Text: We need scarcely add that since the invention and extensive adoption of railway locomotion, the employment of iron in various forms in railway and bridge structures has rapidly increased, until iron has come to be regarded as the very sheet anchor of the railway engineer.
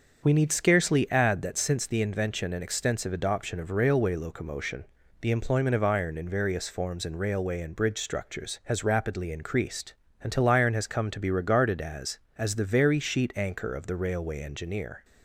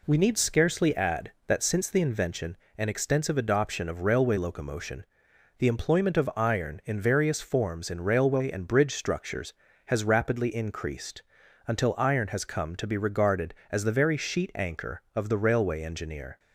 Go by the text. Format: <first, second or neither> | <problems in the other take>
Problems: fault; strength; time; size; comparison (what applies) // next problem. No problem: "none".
second | starts louder than the rest; until 1.2 s; 6.5 dB // says "as" twice; at 12.3 s